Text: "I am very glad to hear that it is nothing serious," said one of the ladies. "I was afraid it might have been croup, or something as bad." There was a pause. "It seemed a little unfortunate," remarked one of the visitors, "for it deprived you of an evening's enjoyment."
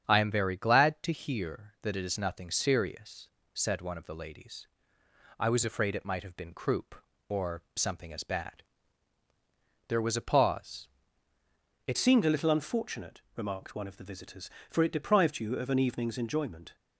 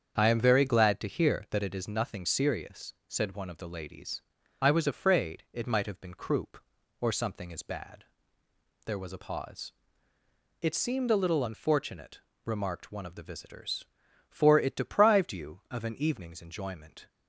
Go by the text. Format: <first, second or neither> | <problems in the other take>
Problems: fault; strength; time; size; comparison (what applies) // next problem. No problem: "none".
second | starts louder than the rest; strong; until 1.0 s; 8 dB; strong in the second // changes voice at "seemed"; from 11.9 s on; 4.8 s long